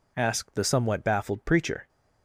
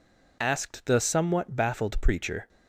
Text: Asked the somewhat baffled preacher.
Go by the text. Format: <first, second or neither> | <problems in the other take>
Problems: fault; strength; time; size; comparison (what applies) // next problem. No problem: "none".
neither | none